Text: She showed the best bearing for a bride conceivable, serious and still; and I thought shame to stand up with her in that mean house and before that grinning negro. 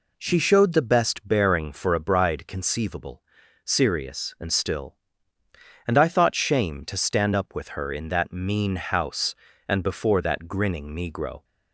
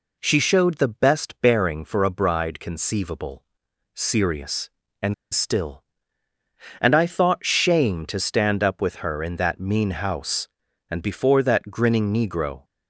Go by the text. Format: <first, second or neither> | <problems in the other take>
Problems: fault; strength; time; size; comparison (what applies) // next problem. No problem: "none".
first | pauses between "and" and "still"; slight; at 5.1 s; 0.19 s long